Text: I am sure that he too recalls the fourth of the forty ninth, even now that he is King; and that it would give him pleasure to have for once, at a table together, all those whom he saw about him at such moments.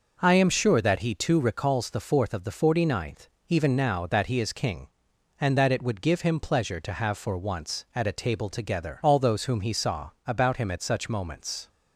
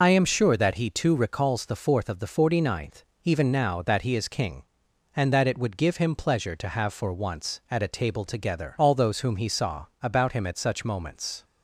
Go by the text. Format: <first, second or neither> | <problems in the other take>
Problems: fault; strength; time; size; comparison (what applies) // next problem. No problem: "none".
first | loses the start of "I"; at 0.0 s; 65 ms // pauses between "saw" and "about"; slight; at 9.8 s; 0.16 s long; slight in the first